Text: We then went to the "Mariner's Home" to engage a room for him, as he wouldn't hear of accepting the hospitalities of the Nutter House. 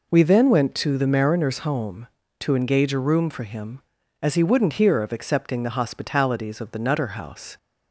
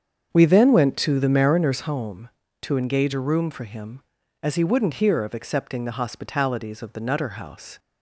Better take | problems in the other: first | starts louder than the rest; strong; until 1.9 s; 7 dB

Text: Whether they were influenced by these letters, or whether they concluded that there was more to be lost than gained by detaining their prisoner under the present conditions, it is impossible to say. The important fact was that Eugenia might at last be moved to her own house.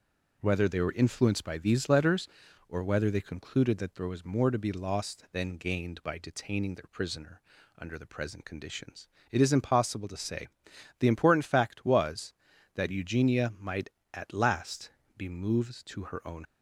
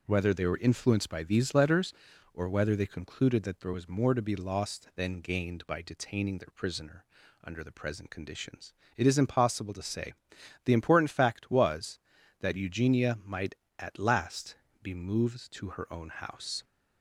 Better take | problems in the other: second | pauses between "prisoner" and "under"; at 7.4 s; 0.38 s long; also in the second // pauses between "last" and "be"; slight; at 14.9 s; 0.26 s long; slight in the second // stops before "house"; at 16.4 s

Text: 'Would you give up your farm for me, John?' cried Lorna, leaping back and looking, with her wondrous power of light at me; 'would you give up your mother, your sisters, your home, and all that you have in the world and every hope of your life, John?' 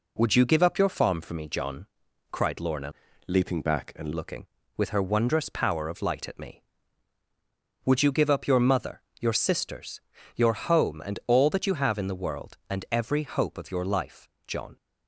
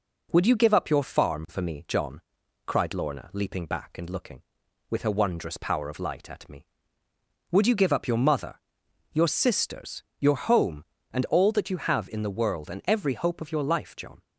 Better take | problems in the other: second | changes voice from "leaping" to "and"; from 3.2 to 4.1 s; 0.9 s long

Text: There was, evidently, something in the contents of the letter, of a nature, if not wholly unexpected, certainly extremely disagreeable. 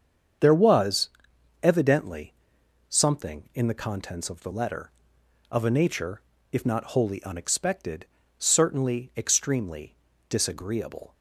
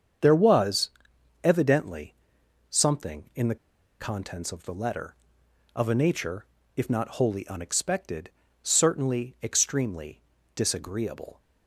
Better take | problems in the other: first | starts louder than the rest; strong; until 1.7 s; 7.5 dB; strong in the first // pauses between "the" and "contents"; at 3.5 s; 0.44 s long // pauses between "extremely" and "disagreeable"; slight; at 10.1 s; 0.36 s long; slight in the first

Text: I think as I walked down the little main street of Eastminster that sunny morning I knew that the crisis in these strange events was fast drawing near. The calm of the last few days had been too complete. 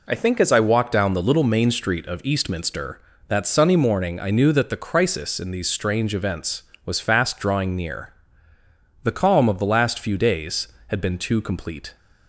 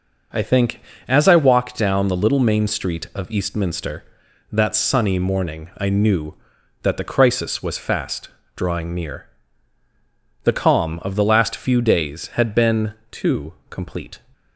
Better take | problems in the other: first | starts louder than the rest; noticeable; until 1.6 s; 6 dB // skips "in these strange events"; at 7.6 s // pauses between "fast" and "drawing"; slight; at 8.2 s; 0.26 s long // pauses between "been" and "too"; slight; at 12.9 s; 0.18 s long // pauses between "too" and "complete"; slight; at 13.5 s; 0.16 s long

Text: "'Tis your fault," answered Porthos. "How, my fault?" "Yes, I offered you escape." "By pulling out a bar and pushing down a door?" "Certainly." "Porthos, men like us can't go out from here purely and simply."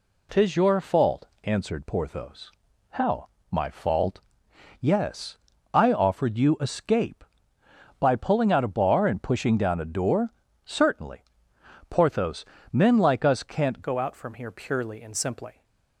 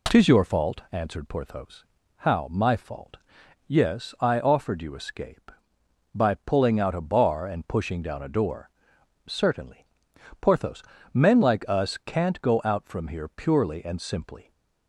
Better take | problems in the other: second | changes voice at "go"; from 13.8 s on; 1.8 s long

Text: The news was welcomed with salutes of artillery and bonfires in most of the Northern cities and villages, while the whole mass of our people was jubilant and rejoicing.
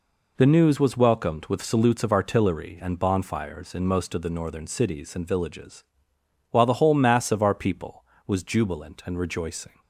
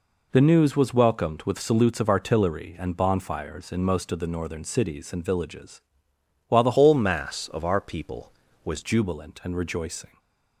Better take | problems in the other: first | changes voice from "whole" to "was"; from 6.7 to 8.8 s; 2.1 s long // stays silent after the last word; slight; from 10.0 s on; 0.6 s long

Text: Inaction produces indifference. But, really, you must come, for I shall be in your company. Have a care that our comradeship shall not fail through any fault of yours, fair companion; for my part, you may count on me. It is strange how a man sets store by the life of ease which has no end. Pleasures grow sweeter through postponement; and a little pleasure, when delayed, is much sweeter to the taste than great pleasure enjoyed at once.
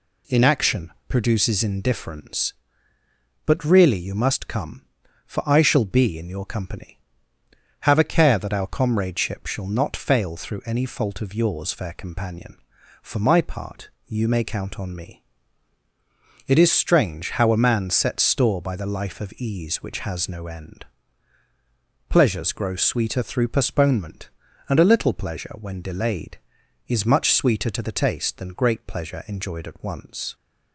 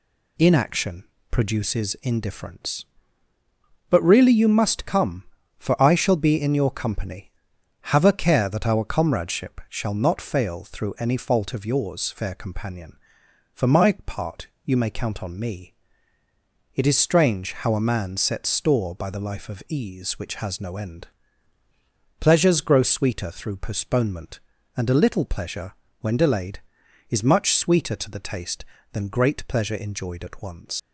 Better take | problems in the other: first | pauses between "Inaction" and "produces"; slight; at 1.0 s; 0.26 s long; slight in the first // leaves "once" unfinished; at 30.7 s; 125 ms

